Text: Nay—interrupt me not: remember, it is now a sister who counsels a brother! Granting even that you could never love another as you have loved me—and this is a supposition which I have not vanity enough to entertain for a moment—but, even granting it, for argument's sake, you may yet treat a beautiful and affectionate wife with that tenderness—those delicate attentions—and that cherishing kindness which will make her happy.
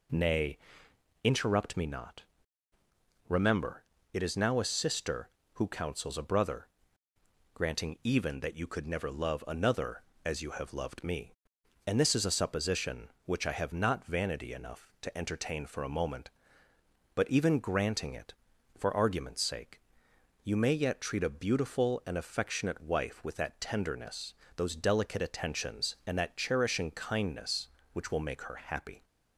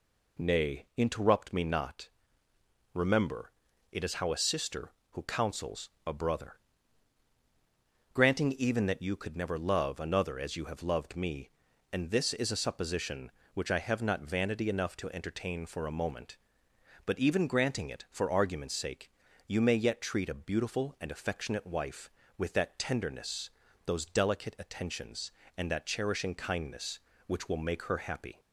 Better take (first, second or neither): first